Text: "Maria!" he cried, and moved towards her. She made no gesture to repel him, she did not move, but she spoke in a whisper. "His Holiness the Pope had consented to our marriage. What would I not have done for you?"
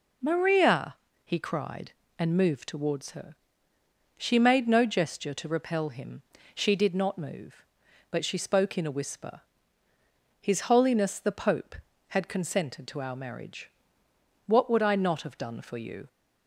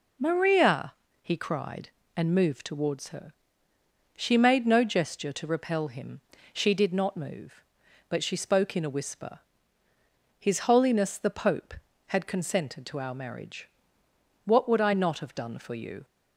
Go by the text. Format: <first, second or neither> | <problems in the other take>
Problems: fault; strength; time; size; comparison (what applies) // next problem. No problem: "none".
neither | none